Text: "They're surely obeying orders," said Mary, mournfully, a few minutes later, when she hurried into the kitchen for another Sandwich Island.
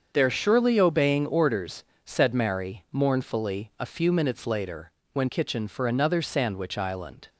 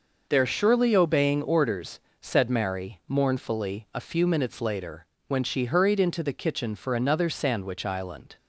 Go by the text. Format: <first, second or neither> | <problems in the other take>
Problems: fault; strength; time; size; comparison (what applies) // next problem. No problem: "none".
second | starts louder than the rest; until 1.1 s; 7 dB // skips "she hurried into the"; at 5.2 s